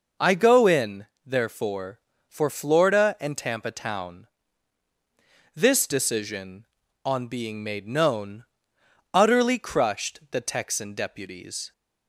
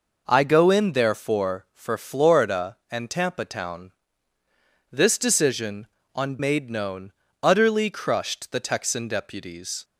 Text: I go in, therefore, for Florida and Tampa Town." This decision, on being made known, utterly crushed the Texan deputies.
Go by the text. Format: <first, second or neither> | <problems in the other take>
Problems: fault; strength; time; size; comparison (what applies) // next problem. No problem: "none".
first | skips "being"; at 6.3 s